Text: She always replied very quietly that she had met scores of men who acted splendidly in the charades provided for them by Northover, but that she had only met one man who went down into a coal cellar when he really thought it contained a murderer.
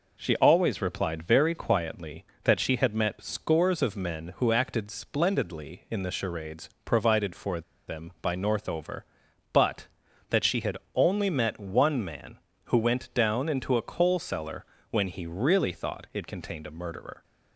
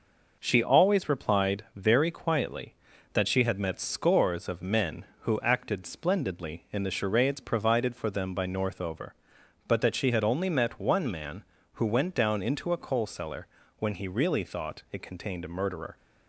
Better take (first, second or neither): second